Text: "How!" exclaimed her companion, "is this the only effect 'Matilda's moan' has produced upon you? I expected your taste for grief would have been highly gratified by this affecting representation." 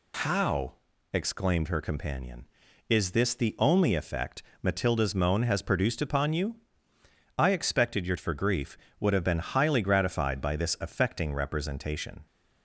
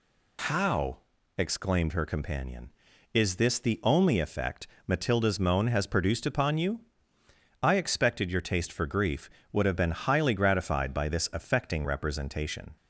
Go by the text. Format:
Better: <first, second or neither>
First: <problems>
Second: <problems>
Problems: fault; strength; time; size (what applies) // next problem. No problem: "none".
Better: second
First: pauses between "effect" and "Matilda's"; slight; at 4.4 s; 0.20 s long // skips "taste"; at 8.1 s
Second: pauses between "effect" and "Matilda's"; slight; at 4.6 s; 0.20 s long